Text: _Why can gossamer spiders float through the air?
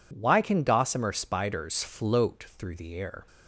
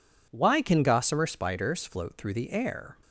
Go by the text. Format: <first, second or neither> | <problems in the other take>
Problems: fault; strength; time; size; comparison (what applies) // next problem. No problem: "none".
neither | none